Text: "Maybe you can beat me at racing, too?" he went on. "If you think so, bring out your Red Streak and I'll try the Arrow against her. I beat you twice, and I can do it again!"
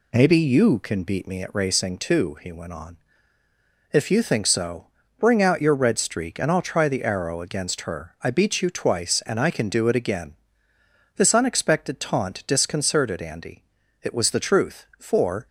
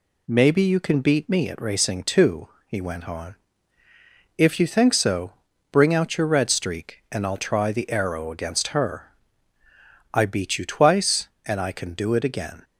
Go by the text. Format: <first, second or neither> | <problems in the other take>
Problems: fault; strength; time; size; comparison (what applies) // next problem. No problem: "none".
second | goes on to say "This unexpected taunt disconcerted Andy It was the truth for"; strong; from 11.1 s on; 4.3 s long